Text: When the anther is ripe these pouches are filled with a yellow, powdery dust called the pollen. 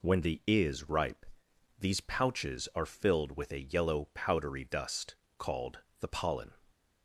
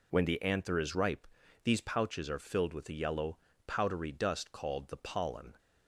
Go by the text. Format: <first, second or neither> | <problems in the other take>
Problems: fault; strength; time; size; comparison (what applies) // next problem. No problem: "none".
second | skips "anther"; at 0.4 s // pauses between "ripe" and "these"; noticeable; at 1.2 s; 0.52 s long; slight in the second // pauses between "dust" and "called"; slight; at 5.1 s; 0.22 s long // pauses between "called" and "the"; slight; at 5.7 s; 0.18 s long